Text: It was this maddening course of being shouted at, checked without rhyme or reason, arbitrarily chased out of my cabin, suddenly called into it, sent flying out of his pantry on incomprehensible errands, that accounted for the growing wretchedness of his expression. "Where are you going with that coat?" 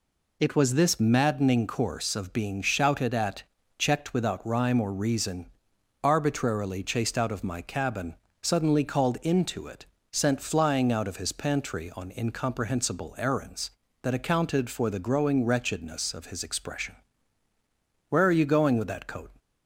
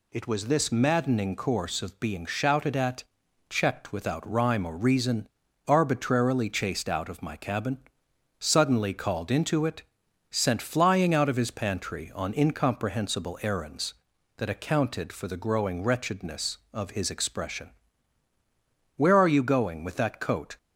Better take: neither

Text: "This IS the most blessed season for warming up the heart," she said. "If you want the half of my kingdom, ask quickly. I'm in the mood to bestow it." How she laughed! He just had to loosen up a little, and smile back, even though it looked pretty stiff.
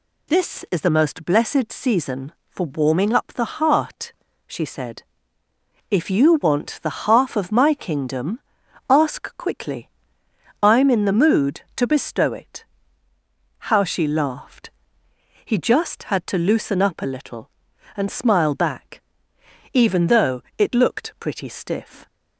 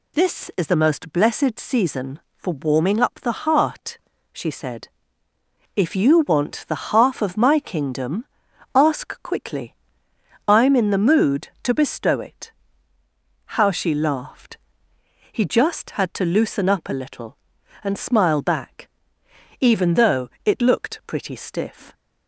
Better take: neither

